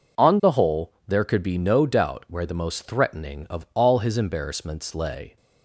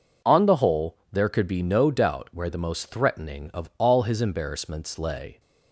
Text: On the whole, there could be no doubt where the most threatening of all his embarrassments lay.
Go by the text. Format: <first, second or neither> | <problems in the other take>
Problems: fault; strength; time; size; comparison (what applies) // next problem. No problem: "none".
neither | none